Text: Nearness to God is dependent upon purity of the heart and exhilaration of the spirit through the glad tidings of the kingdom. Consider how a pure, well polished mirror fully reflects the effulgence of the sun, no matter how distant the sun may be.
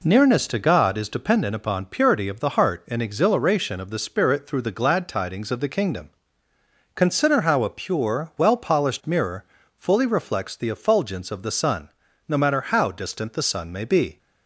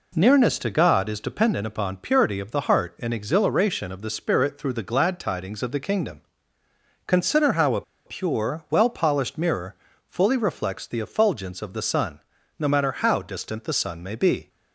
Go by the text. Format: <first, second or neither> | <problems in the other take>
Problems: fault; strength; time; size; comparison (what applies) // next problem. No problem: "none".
first | pauses between "a" and "pure"; slight; at 7.8 s; 0.24 s long // pauses between "mirror" and "fully"; slight; at 9.7 s; 0.32 s long; slight in the first